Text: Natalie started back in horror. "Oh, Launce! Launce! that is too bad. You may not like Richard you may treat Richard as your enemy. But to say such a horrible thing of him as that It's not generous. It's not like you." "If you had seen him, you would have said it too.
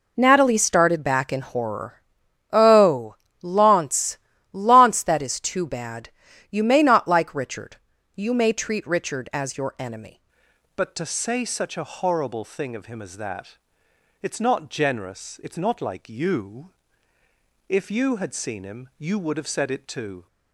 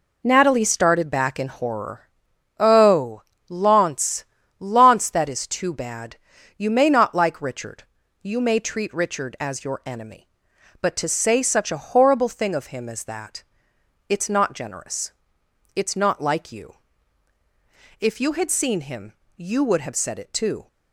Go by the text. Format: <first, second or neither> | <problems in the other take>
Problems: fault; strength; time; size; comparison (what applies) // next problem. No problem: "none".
second | pauses between "Richard" and "you"; at 7.7 s; 0.40 s long; also in the second // changes voice at "But"; from 10.7 s on; 9.5 s long // pauses between "that" and "It's"; noticeable; at 13.5 s; 0.64 s long; noticeable in the second